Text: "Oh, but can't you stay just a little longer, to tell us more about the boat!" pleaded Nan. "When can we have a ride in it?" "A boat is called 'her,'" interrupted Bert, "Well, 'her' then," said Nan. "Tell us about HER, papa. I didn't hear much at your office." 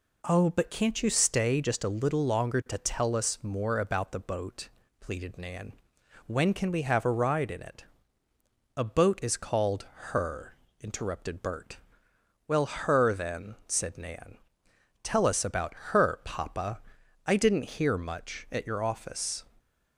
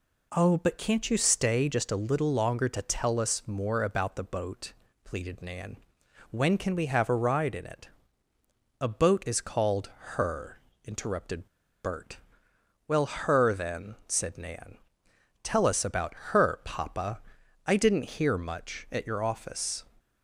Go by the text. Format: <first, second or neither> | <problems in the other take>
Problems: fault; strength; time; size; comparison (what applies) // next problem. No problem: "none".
first | pauses between "interrupted" and "Bert"; at 11.4 s; 0.38 s long // pauses between "about" and "HER"; slight; at 16.1 s; 0.18 s long; slight in the first